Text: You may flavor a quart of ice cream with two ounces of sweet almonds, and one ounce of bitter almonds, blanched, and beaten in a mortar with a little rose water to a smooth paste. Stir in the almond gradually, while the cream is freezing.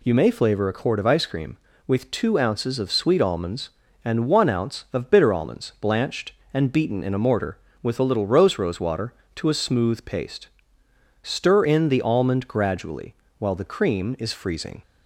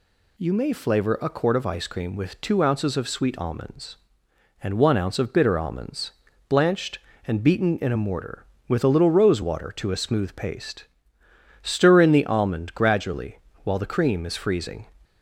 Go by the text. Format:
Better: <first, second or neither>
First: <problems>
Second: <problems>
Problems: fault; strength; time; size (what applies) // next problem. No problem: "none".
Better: second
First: says "rose" twice; at 8.5 s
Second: none